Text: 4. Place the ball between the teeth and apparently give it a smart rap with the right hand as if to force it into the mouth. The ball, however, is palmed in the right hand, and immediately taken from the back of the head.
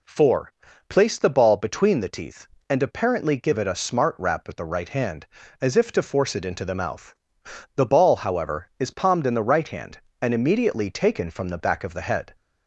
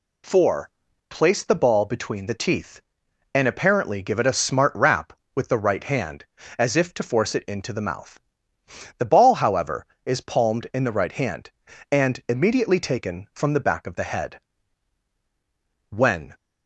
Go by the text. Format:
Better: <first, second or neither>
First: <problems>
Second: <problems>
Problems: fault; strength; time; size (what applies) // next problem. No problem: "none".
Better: first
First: none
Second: goes on to say "When"; slight; from 15.9 s on; 0.42 s long